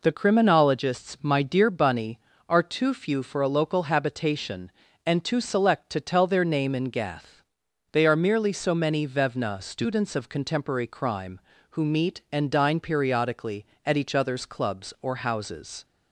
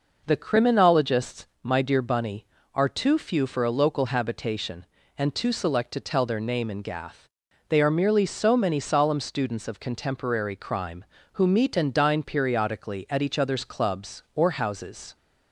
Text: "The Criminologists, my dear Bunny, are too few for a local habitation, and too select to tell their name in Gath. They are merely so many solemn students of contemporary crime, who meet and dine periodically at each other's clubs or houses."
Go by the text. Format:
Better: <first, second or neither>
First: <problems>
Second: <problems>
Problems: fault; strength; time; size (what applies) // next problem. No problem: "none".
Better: second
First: says "vevna" for "solemn"; at 9.0 s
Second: none